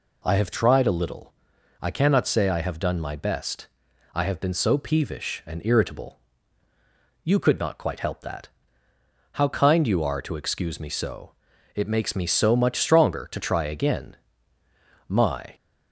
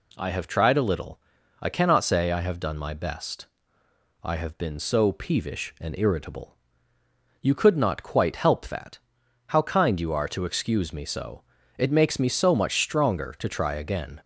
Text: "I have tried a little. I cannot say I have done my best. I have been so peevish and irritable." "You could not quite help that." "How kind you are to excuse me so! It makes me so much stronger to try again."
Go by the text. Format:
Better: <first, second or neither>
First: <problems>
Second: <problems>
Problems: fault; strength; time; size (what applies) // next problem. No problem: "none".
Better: second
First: goes on to say "My"; slight; from 15.0 s on; 0.46 s long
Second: none